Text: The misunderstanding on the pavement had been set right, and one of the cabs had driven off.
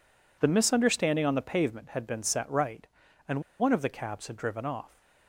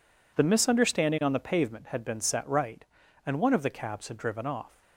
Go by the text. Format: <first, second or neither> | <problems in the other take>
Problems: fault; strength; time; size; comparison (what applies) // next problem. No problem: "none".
second | pauses between "and" and "one"; slight; at 3.4 s; 0.18 s long